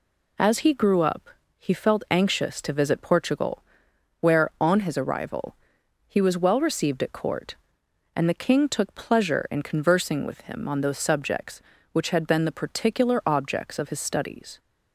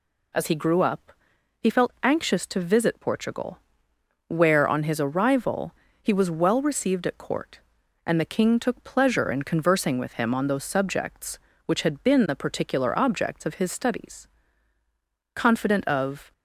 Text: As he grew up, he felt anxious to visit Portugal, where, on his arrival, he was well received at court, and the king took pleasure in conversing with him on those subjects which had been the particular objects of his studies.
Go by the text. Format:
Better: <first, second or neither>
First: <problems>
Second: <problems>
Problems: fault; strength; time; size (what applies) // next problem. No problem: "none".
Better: first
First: none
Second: goes on to say "Confident of"; noticeable; from 15.3 s on; 0.96 s long